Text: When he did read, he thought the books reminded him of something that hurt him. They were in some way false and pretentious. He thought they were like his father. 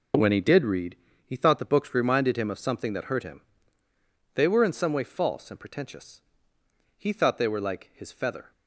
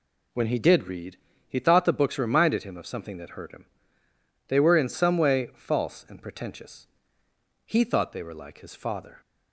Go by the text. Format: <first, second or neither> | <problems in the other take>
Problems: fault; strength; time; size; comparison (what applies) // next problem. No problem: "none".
second | says "feather" for "father"; at 8.1 s